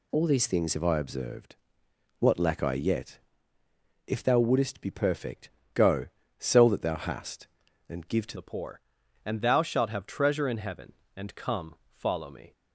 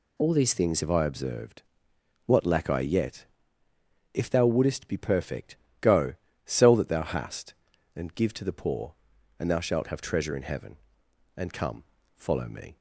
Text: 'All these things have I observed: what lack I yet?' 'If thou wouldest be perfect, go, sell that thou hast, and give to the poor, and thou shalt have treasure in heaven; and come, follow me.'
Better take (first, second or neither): second